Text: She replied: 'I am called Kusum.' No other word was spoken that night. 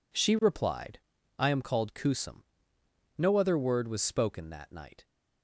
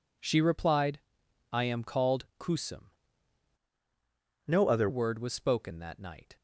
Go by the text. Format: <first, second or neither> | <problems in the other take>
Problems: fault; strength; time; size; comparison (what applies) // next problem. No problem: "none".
first | changes voice from "No" to "other"; from 4.4 to 4.8 s; 0.4 s long